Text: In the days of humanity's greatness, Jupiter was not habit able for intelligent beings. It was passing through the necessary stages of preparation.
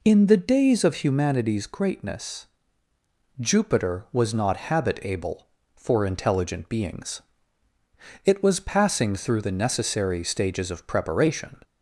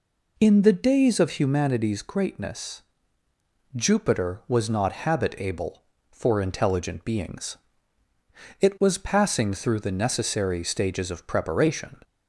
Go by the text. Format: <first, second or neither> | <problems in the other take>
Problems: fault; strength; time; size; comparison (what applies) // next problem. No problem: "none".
neither | none